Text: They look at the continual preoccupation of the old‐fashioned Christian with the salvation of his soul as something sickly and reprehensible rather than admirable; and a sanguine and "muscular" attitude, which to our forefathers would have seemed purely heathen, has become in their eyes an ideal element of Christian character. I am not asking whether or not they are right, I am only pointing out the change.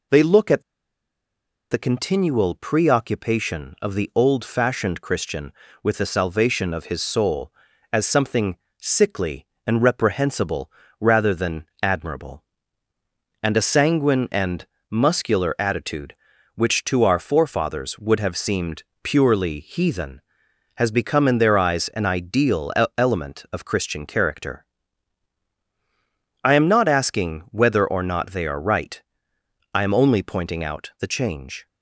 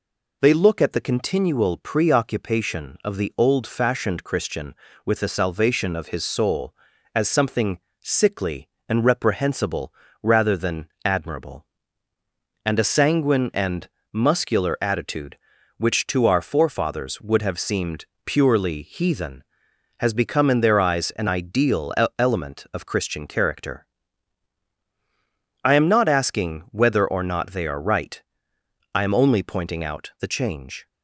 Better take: second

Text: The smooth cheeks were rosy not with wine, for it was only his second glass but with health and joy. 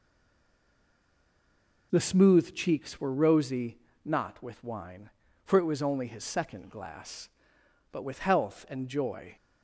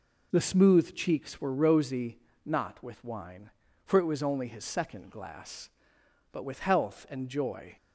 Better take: second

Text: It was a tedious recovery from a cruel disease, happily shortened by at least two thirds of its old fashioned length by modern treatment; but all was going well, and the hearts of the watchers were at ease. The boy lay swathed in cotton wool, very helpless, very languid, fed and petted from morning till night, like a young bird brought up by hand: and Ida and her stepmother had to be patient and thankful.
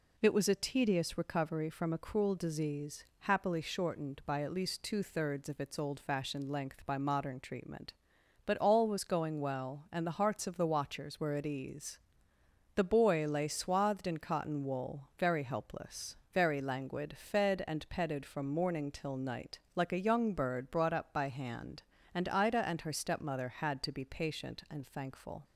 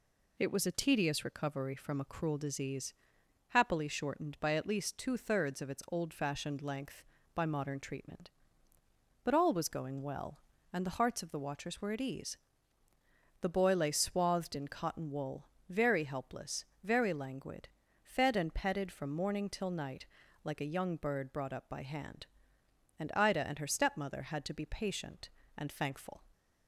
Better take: neither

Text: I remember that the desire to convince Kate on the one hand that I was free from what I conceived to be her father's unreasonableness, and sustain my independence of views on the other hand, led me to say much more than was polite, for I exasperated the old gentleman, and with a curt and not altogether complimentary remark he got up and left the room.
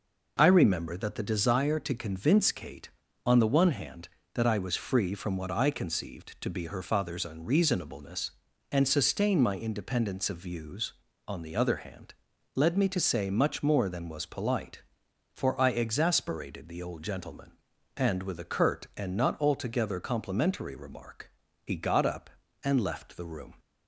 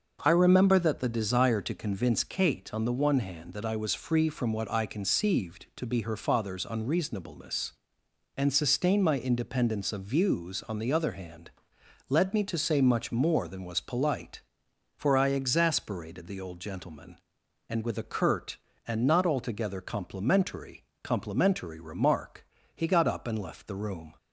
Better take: first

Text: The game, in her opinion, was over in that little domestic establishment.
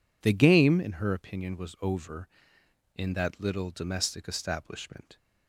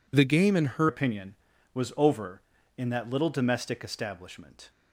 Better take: first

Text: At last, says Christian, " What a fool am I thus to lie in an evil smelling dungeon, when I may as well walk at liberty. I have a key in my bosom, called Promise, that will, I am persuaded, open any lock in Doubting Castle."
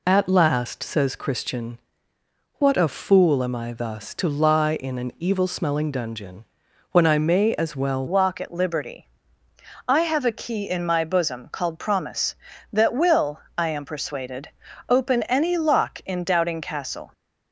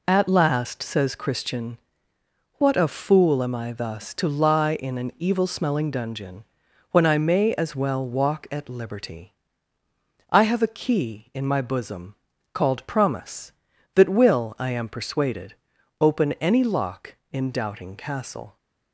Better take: second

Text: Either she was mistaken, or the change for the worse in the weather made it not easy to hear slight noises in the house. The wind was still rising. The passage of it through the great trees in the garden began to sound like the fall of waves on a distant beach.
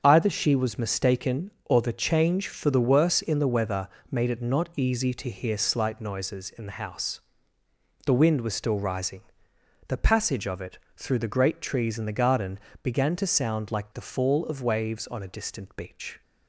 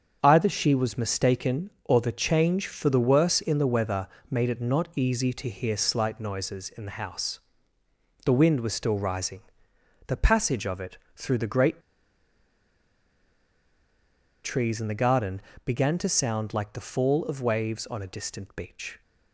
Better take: first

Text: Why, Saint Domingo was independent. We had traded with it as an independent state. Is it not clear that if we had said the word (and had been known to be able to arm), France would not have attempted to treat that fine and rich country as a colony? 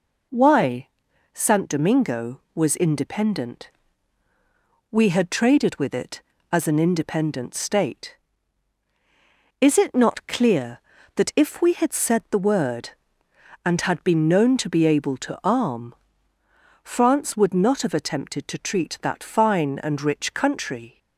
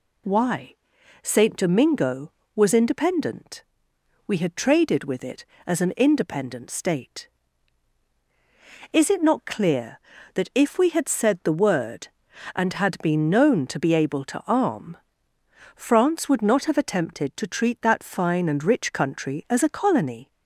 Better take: second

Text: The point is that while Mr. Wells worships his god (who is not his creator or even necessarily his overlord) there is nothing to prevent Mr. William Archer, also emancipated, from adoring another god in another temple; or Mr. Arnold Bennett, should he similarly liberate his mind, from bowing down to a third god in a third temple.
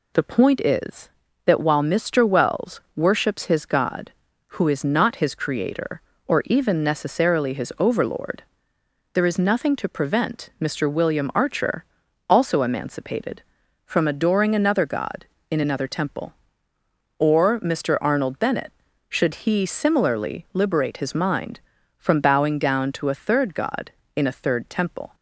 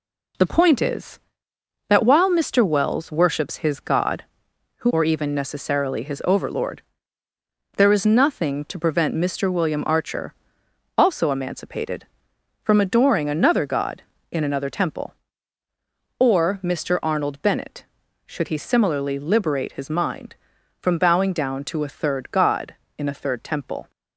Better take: first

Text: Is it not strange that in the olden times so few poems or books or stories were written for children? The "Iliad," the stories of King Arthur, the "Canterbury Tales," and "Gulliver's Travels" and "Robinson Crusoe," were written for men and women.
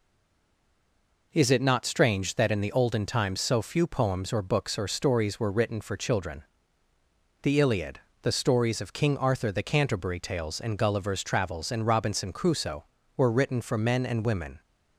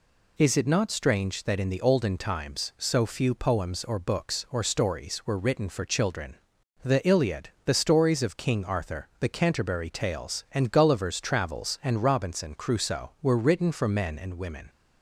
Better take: second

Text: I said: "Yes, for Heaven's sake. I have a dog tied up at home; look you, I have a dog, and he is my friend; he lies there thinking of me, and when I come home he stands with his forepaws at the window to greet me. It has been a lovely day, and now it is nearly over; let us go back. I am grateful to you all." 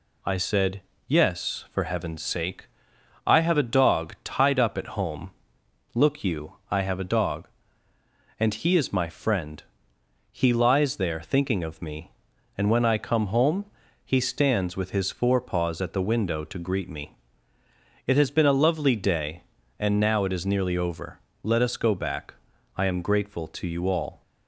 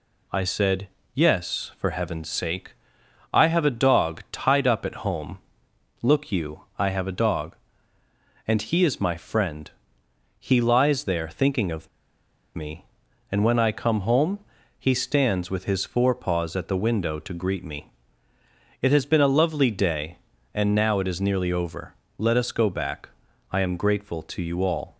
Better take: first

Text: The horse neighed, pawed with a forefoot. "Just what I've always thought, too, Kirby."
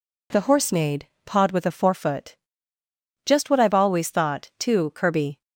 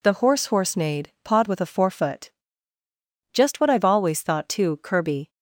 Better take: first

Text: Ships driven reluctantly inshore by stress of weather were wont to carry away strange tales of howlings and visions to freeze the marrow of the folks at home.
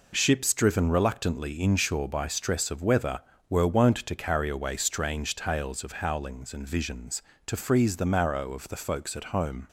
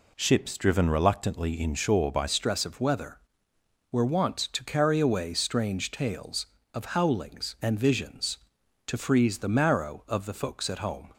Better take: first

